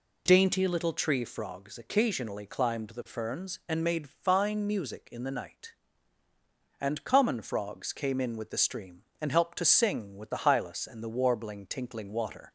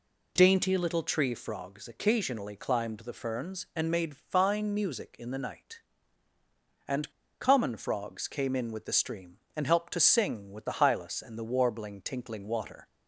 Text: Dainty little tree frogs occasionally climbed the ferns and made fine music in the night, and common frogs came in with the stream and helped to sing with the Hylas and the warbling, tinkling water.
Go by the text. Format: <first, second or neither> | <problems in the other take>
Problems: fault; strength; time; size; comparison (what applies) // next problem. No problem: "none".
first | pauses between "and" and "common"; slight; at 7.1 s; 0.29 s long